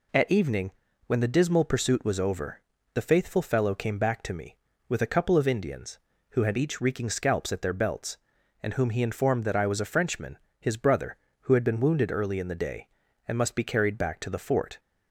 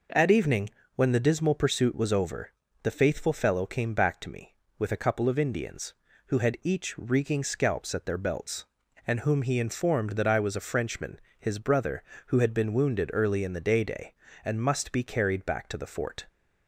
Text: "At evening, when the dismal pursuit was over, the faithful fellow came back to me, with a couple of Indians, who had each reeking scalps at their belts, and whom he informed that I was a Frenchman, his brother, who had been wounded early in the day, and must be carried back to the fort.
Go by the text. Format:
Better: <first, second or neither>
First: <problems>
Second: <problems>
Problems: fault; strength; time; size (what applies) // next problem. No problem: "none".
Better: first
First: none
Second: says "day" twice; at 13.8 s